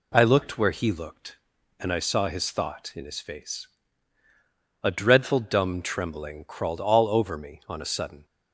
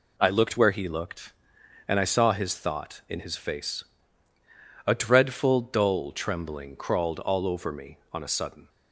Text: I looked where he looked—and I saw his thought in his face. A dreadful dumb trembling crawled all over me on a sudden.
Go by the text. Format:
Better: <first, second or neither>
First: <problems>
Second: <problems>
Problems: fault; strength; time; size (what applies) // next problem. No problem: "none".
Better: first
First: none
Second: says "dull" for "dumb"; at 5.6 s